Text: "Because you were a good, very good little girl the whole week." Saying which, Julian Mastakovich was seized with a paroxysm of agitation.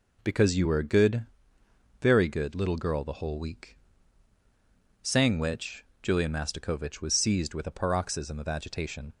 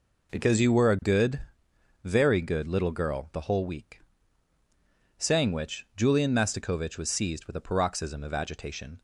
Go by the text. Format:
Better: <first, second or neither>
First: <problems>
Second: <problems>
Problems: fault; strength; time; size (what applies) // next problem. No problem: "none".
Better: neither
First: none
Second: none